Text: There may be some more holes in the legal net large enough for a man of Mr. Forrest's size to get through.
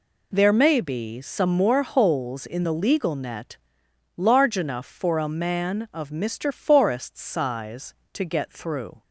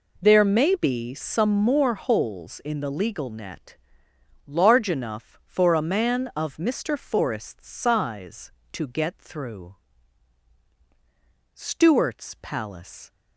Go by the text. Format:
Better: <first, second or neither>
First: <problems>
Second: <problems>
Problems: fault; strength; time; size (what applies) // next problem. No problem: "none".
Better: first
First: pauses between "net" and "large"; noticeable; at 3.5 s; 0.58 s long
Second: pauses between "net" and "large"; noticeable; at 3.7 s; 0.70 s long // goes on to say "STEWART'S PALACE"; from 11.5 s on; 1.5 s long